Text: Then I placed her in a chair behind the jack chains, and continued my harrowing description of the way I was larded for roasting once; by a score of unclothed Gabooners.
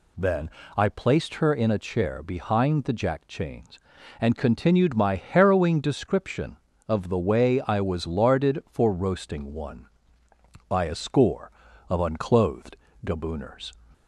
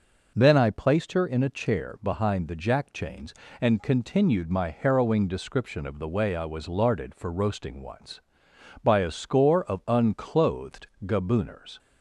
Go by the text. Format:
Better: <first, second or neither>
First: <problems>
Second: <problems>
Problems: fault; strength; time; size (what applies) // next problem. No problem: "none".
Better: second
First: pauses between "Then" and "I"; slight; at 0.4 s; 0.26 s long // says "one" for "once"; at 9.5 s // pauses between "unclothed" and "Gabooners"; slight; at 12.7 s; 0.30 s long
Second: pauses between "unclothed" and "Gabooners"; slight; at 10.8 s; 0.18 s long